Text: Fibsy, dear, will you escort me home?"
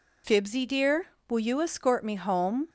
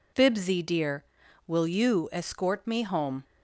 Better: neither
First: none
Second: none

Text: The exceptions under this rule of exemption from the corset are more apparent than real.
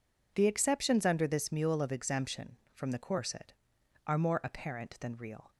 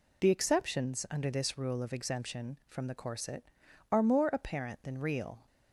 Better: second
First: says "mule" for "rule"; at 1.5 s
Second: none

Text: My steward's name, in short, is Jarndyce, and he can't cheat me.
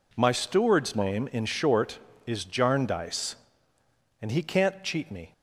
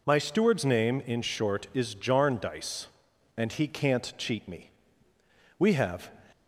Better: first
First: none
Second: goes on to say "We have"; from 5.5 s on; 0.56 s long

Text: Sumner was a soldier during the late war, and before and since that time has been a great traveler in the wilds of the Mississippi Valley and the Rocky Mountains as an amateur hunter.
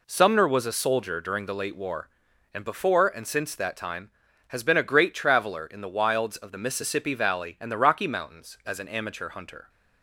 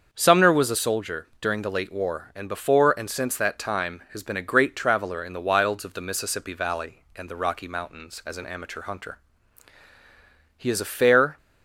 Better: first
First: none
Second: starts louder than the rest; until 1.1 s; 6.5 dB // goes on to say "He is a fair"; noticeable; from 10.5 s on; 0.78 s long

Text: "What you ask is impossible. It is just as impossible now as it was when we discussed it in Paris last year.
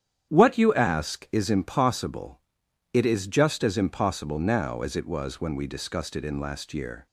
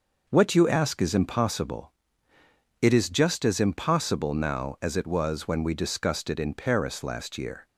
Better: second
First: starts louder than the rest; strong; until 1.3 s; 9.5 dB // skips "Paris"; at 6.3 s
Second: none

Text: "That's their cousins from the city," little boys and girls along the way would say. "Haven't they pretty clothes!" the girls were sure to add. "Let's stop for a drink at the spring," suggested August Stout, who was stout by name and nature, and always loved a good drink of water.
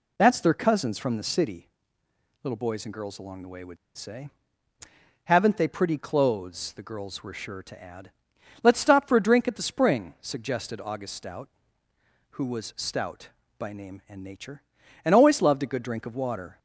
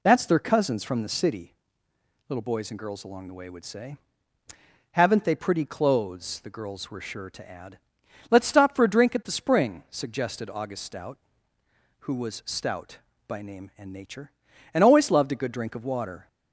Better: second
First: pauses between "would" and "say"; slight; at 3.7 s; 0.21 s long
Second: none

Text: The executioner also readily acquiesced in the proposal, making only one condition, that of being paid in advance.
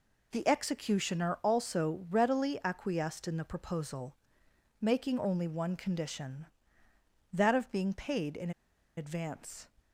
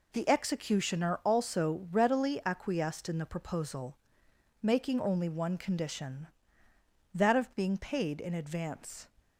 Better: second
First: pauses between "in" and "advance"; noticeable; at 8.5 s; 0.46 s long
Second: none

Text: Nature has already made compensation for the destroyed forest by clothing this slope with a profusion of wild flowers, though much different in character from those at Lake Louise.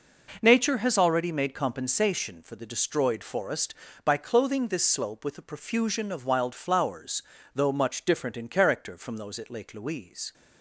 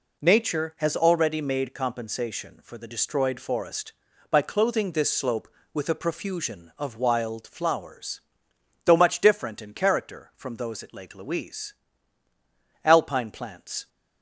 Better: first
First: none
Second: goes on to say "Alpine plants"; noticeable; from 12.8 s on; 1.0 s long

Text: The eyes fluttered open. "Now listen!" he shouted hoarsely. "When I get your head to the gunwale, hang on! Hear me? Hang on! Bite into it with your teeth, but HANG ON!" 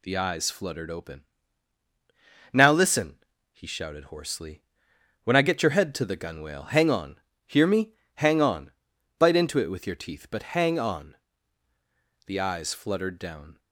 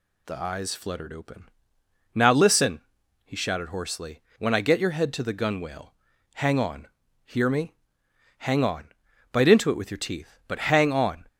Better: second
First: goes on to say "The eyes fluttered down"; from 12.2 s on; 1.3 s long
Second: none

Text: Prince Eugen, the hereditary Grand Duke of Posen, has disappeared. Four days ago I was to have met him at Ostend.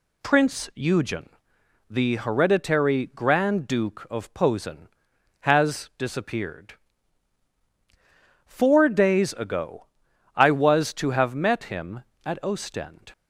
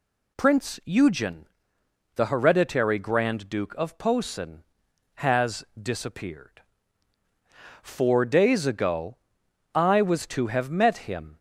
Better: first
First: pauses between "ago" and "I"; noticeable; at 9.8 s; 0.50 s long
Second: pauses between "has" and "disappeared"; slight; at 5.6 s; 0.16 s long // pauses between "ago" and "I"; noticeable; at 9.1 s; 0.58 s long // stops before "at Ostend"; at 11.3 s

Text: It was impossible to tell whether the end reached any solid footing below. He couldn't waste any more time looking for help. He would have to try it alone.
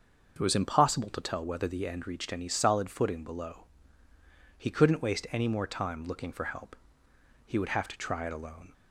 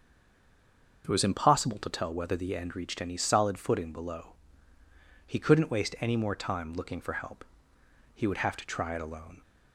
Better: first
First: starts louder than the rest; until 1.3 s; 6.5 dB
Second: stays silent before the first word; until 1.0 s; 1.0 s long // starts louder than the rest; until 2.0 s; 6.5 dB

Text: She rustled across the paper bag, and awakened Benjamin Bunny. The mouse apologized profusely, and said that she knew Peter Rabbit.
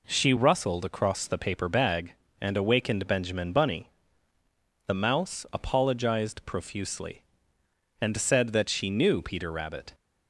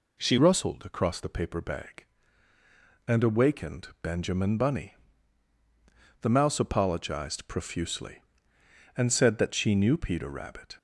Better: first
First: none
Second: changes voice at "rustled"; from 0.3 s on; 10.4 s long

